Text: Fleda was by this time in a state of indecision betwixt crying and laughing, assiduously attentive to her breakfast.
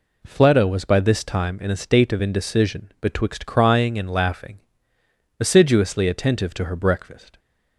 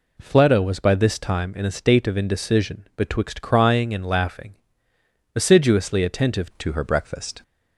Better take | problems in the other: first | changes voice at "to"; from 6.6 s on; 0.8 s long

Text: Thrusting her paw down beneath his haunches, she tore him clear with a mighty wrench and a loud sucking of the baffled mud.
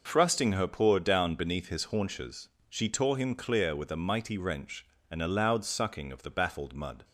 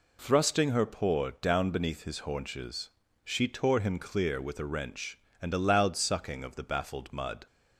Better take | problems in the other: first | skips "mighty"; at 4.6 s

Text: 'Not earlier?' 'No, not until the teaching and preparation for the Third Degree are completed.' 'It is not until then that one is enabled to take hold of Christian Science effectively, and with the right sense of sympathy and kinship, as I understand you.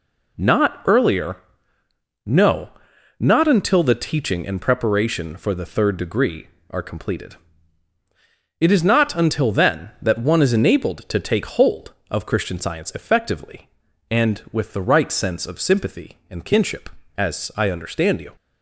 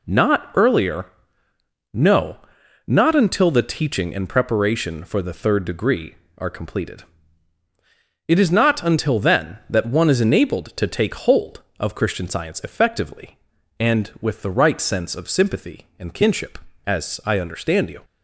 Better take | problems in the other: neither | none

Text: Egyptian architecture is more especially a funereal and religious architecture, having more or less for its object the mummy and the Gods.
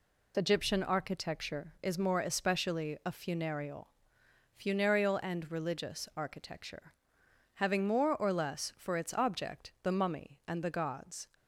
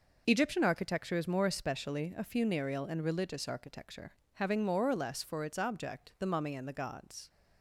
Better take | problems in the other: second | says "funereal" twice; at 4.5 s

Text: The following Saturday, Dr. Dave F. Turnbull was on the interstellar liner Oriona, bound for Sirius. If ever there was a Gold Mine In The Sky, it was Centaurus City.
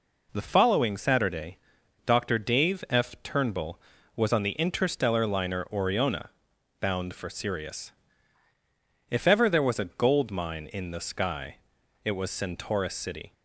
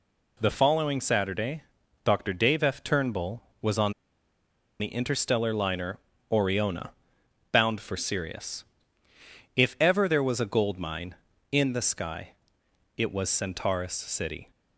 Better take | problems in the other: first | pauses between "on" and "the"; noticeable; at 3.9 s; 0.87 s long // pauses between "liner" and "Oriona"; slight; at 5.9 s; 0.32 s long

